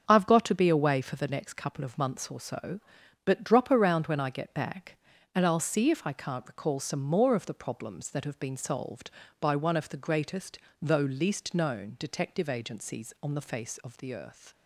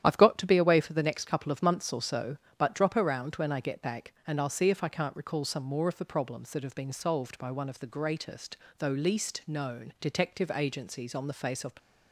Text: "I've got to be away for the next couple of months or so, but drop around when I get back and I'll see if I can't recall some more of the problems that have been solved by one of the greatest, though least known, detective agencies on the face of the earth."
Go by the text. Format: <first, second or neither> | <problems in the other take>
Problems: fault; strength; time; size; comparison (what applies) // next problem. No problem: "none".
first | starts louder than the rest; strong; until 1.0 s; 10.5 dB; also in the first // stops before "the earth"; at 11.7 s